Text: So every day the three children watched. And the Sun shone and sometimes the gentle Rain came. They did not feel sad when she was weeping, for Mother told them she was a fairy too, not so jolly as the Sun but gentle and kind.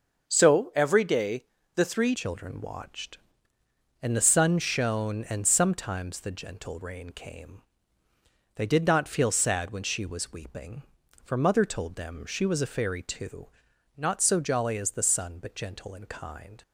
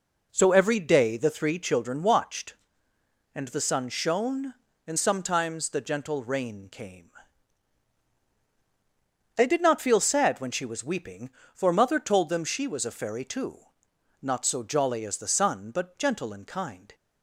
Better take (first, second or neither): second